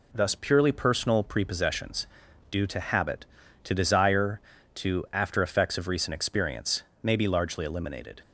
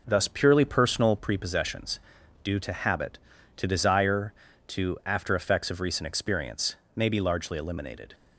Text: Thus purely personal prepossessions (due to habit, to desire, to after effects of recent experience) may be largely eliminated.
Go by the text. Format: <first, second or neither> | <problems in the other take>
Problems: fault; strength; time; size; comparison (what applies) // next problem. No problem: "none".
first | starts louder than the rest; noticeable; until 1.3 s; 5.5 dB